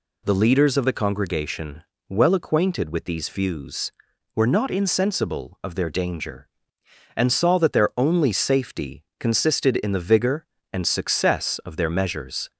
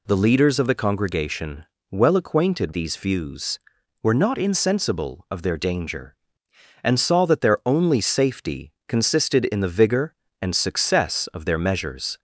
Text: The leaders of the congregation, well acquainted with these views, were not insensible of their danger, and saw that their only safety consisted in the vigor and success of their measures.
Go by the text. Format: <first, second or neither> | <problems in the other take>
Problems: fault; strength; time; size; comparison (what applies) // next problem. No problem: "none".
first | skips "with"; at 2.7 s // pauses between "safety" and "consisted"; slight; at 8.7 s; 0.16 s long; slight in the first